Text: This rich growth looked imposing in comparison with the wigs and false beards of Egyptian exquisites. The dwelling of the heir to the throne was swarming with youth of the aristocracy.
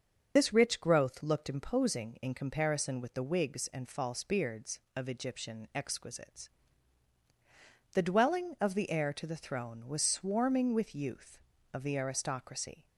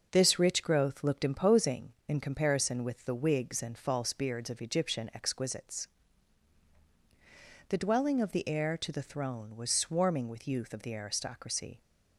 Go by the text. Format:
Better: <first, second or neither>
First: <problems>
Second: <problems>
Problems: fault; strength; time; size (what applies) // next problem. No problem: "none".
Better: second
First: loses the start of "This"; at 0.3 s; 35 ms // starts louder than the rest; until 1.3 s; 6.5 dB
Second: none